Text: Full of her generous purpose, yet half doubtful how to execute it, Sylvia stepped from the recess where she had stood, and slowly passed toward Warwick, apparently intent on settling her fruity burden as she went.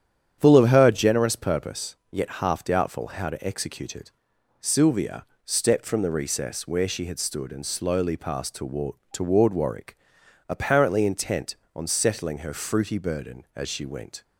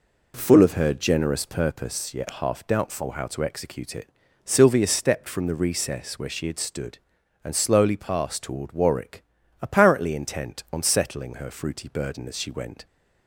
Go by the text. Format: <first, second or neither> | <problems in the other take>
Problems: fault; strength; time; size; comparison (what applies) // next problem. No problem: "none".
second | starts louder than the rest; strong; until 1.4 s; 9.5 dB // pauses between "Sylvia" and "stepped"; slight; at 5.2 s; 0.18 s long // says "toward" twice; at 9.1 s